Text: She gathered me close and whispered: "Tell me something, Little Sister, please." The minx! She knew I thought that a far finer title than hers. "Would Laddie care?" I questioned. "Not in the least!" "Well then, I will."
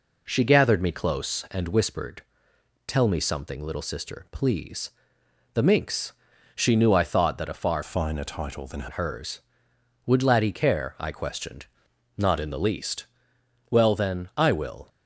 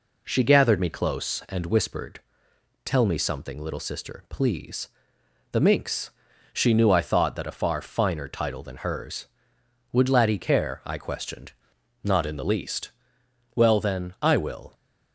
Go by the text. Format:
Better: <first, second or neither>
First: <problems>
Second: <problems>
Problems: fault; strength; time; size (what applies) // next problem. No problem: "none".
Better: second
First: changes voice from "finer" to "than"; from 7.8 to 8.8 s; 1.0 s long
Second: none